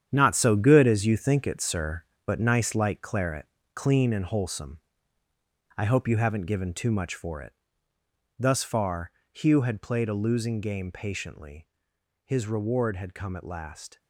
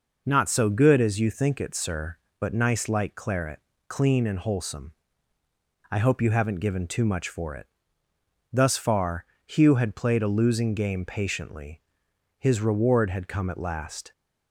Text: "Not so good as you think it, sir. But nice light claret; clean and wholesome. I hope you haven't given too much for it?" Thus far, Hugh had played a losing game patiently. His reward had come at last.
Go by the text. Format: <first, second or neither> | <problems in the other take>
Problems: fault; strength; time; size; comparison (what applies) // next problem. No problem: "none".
second | gets quieter; strong; throughout; 10.5 dB